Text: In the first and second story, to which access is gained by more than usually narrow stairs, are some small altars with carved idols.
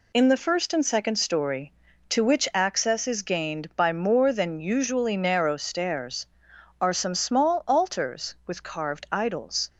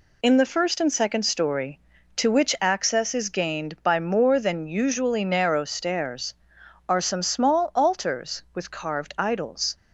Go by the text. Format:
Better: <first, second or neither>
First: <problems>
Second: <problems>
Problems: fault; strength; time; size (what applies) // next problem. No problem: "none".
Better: neither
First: none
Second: none